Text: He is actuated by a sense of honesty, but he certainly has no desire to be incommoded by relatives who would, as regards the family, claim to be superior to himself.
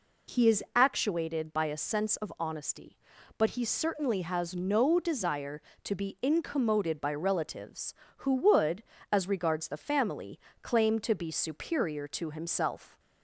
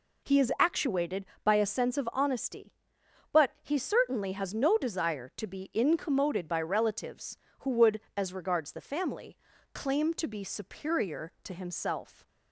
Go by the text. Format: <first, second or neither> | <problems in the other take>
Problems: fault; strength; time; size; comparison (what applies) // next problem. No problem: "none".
neither | none